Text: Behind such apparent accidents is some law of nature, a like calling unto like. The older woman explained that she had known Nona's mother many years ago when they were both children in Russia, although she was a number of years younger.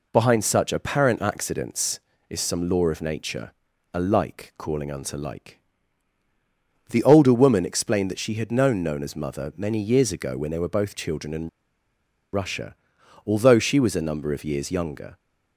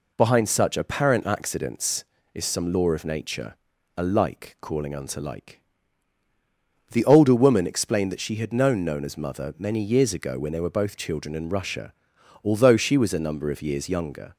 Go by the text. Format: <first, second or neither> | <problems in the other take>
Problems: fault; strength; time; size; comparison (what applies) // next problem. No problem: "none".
second | pauses between "in" and "Russia"; noticeable; at 11.4 s; 0.86 s long